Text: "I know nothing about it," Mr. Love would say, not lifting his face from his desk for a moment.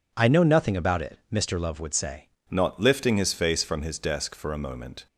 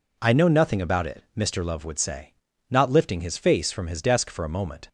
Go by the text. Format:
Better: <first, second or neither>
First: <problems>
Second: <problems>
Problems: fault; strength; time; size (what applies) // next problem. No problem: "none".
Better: second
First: changes voice at "not"; from 2.5 s on; 2.5 s long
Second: none